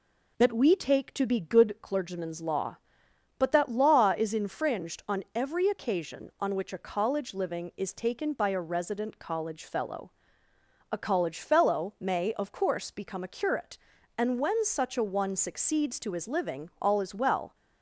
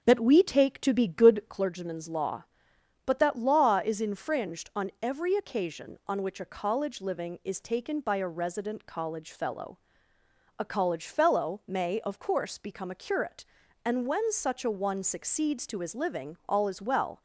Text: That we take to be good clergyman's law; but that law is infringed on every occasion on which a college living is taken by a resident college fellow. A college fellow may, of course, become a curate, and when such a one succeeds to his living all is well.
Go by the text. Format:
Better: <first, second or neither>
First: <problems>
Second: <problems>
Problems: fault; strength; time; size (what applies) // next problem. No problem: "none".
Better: first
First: none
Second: starts louder than the rest; strong; until 1.7 s; 7.5 dB